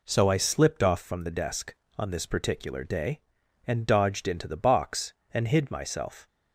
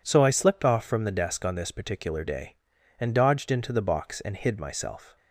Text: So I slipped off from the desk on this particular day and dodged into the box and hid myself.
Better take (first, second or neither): neither